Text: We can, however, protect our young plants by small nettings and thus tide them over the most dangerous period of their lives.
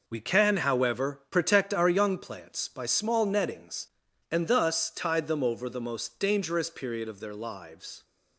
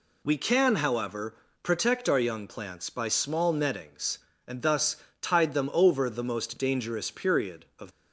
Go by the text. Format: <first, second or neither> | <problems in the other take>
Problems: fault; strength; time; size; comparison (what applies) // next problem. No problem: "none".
first | pauses between "thus" and "tide"; slight; at 4.9 s; 0.24 s long // stops before "their lives"; at 7.9 s